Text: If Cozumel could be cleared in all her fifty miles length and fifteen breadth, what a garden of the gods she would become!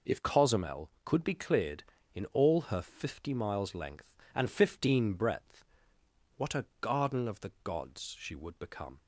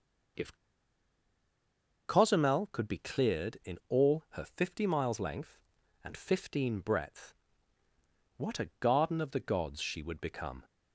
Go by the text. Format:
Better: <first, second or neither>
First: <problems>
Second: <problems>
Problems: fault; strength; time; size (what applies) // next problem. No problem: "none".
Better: first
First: none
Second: pauses between "If" and "Cozumel"; strong; at 0.5 s; 1.5 s long